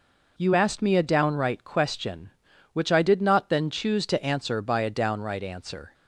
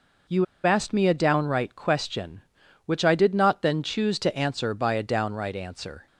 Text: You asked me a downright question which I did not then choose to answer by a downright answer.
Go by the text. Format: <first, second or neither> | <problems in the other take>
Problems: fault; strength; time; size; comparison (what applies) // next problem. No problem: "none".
first | pauses between "You" and "asked"; slight; at 0.4 s; 0.19 s long